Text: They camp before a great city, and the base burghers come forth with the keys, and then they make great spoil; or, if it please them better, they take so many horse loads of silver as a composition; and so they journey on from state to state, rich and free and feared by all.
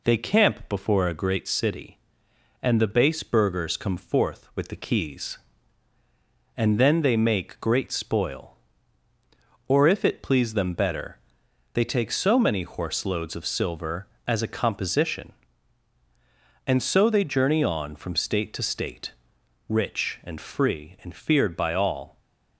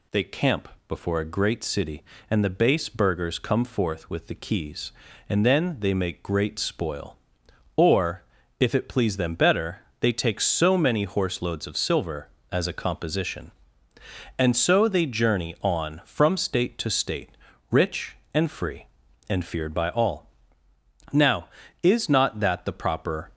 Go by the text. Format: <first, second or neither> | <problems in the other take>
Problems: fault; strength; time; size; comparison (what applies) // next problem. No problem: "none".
first | pauses between "camp" and "before"; slight; at 0.6 s; 0.20 s long // goes on to say "Now is not that the proper"; strong; from 21.1 s on; 2.2 s long